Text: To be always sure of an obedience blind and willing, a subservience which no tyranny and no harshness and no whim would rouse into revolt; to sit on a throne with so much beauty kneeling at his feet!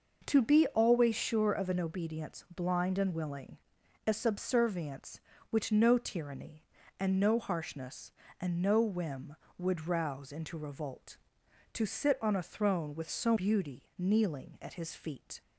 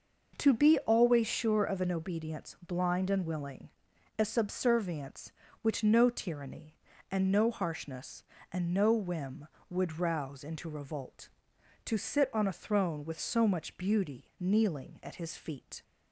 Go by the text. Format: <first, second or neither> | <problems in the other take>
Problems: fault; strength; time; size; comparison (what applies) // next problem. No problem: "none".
second | skips "much"; at 13.3 s